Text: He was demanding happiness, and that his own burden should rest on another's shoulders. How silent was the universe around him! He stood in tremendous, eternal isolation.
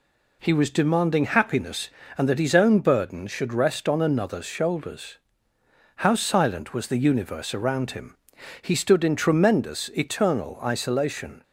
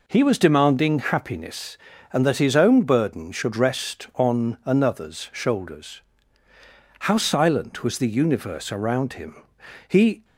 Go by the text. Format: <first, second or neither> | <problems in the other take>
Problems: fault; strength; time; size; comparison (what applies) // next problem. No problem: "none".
first | stops before "stood in tremendous eternal isolation"; at 10.2 s